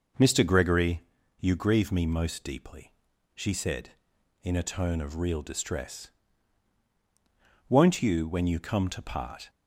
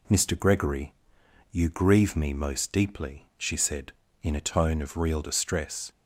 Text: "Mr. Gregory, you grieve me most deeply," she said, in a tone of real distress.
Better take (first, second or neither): second